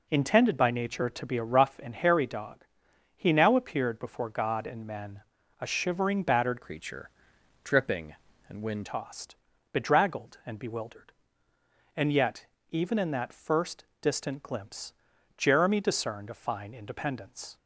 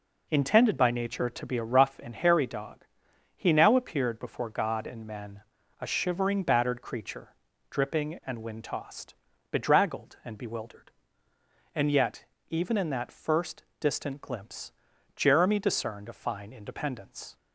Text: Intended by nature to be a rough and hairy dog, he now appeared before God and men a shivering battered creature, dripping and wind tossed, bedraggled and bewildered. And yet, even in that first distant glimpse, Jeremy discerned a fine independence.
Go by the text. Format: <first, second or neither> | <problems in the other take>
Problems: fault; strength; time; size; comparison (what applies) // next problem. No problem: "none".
second | pauses between "men" and "a"; at 5.1 s; 0.40 s long; also in the second // changes voice from "creature" to "wind"; from 6.6 to 8.8 s; 2.2 s long // pauses between "first" and "distant"; slight; at 13.8 s; 0.16 s long; slight in the second